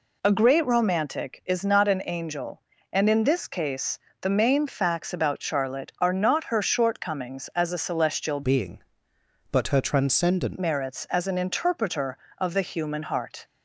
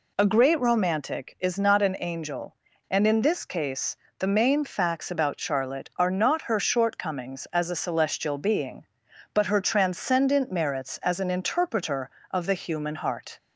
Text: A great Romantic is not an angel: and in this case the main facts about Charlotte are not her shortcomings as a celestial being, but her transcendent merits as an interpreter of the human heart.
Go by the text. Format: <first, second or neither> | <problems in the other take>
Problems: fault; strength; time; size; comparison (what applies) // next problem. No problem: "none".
second | pauses between "case" and "the"; slight; at 3.9 s; 0.22 s long; slight in the second // changes voice from "being" to "transcendent"; from 8.4 to 10.5 s; 2.1 s long